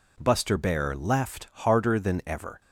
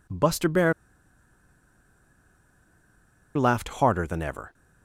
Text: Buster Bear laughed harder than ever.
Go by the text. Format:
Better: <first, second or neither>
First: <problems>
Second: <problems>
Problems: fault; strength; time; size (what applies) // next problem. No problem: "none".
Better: first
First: none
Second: pauses between "Bear" and "laughed"; strong; at 0.7 s; 2.6 s long